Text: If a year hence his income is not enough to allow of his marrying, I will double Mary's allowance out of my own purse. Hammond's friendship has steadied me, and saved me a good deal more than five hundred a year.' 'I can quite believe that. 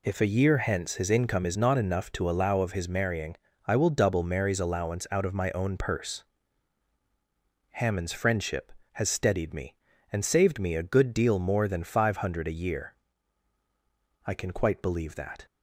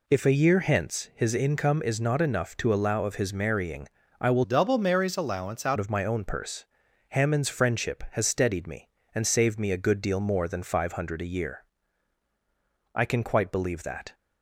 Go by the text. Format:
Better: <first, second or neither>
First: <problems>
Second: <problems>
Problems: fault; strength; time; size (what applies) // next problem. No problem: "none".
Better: first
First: none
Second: changes voice from "double" to "out"; from 4.4 to 5.7 s; 1.3 s long